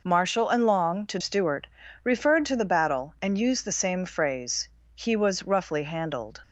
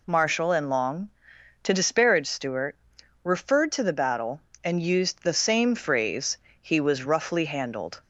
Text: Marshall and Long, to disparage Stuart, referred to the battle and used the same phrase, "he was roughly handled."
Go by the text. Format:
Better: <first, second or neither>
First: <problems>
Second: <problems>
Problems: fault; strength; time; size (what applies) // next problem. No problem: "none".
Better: second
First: skips "disparage"; at 1.1 s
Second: none